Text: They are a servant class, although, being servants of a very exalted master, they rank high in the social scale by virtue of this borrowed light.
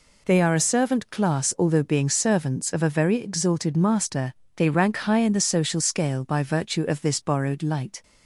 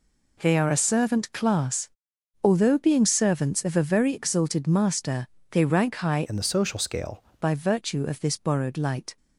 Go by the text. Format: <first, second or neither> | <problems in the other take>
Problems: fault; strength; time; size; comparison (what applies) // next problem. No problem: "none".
first | changes voice from "in" to "scale"; from 6.2 to 7.2 s; 1.0 s long